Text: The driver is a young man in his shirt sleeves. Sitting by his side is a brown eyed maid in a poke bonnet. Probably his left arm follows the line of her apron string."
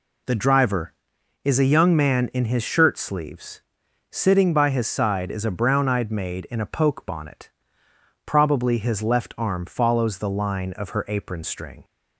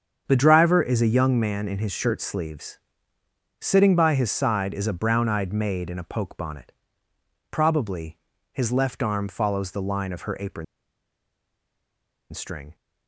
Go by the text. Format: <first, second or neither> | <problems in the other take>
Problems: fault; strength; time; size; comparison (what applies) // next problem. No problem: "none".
first | starts louder than the rest; strong; until 1.2 s; 7.5 dB // pauses between "Probably" and "his"; slight; at 8.1 s; 0.34 s long // pauses between "apron" and "string"; strong; at 10.6 s; 1.6 s long